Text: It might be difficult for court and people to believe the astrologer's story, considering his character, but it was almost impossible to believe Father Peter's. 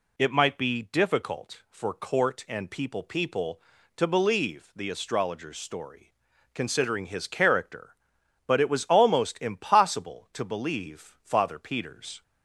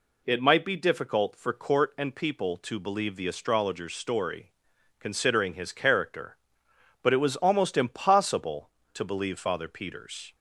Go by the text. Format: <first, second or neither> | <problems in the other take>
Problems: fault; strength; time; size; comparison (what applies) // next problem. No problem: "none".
second | says "people" twice; at 3.0 s